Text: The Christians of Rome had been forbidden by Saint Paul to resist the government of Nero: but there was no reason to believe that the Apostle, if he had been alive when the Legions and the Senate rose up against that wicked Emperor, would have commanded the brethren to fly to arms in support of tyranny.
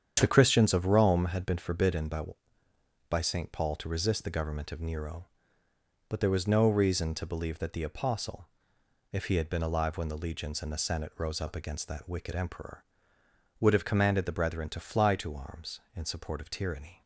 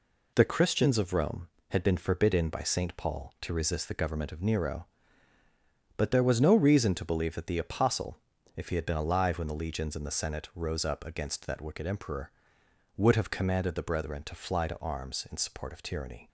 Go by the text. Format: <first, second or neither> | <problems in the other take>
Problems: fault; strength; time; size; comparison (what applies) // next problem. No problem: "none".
second | starts louder than the rest; strong; until 1.2 s; 8.5 dB // says "by" twice; at 3.0 s